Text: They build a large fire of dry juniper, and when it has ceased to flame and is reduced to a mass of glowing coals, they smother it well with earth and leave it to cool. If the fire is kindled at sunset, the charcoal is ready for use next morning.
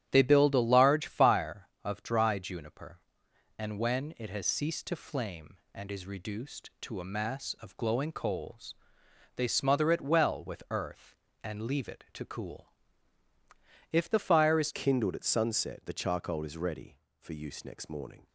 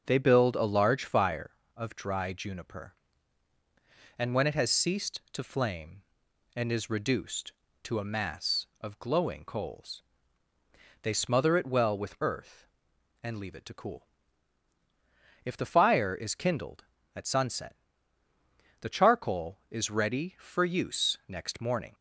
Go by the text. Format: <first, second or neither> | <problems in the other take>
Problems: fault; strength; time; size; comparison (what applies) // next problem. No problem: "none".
second | starts louder than the rest; strong; until 1.1 s; 10.5 dB; also in the second // changes voice at "kindled"; from 14.7 s on; 3.5 s long